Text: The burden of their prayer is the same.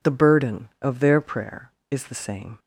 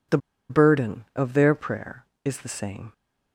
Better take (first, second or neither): first